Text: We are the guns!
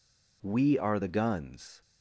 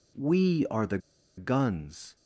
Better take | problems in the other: first | pauses between "the" and "guns"; at 0.9 s; 0.38 s long

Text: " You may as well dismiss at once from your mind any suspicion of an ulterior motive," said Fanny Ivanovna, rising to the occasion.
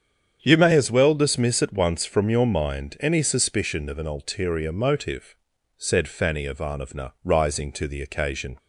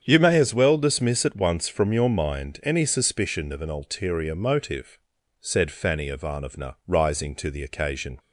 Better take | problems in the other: neither | starts louder than the rest; strong; the same in both

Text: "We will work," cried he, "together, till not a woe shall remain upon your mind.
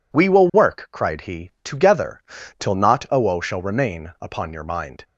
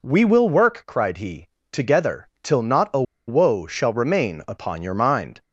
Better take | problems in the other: first | pauses between "a" and "woe"; slight; at 3.0 s; 0.25 s long

